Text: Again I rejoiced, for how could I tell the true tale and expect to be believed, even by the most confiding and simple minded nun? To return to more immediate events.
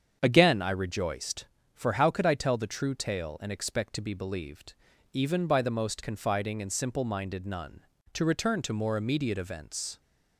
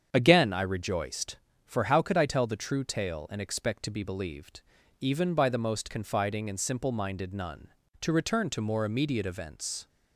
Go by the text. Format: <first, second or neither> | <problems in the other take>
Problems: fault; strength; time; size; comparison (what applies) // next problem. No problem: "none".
neither | starts louder than the rest; strong; the same in both